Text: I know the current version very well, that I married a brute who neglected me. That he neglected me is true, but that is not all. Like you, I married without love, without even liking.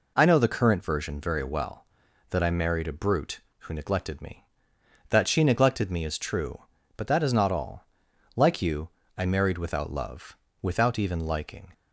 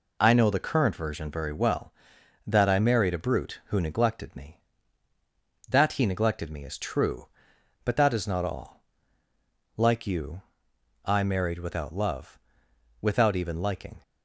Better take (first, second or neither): second